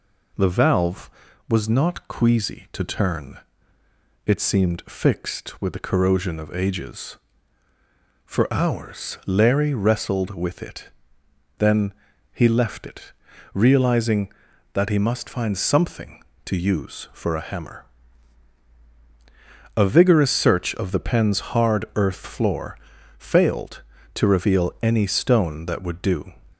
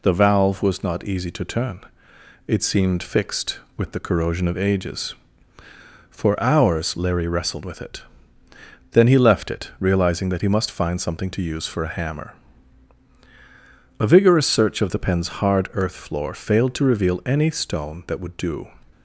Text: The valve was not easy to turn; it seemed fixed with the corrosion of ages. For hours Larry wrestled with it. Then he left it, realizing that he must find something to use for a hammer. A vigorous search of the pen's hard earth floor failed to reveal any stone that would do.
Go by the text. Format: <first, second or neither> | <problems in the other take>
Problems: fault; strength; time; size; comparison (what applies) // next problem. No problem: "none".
second | says "queasy" for "easy"; at 2.0 s // pauses between "Then" and "he"; at 11.9 s; 0.40 s long // pauses between "floor" and "failed"; at 22.7 s; 0.42 s long